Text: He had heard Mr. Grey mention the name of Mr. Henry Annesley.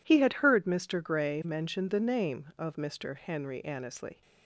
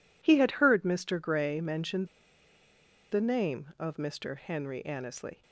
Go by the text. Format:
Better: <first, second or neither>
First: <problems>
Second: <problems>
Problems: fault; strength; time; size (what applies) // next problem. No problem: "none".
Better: first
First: none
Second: pauses between "mention" and "the"; at 2.0 s; 1.0 s long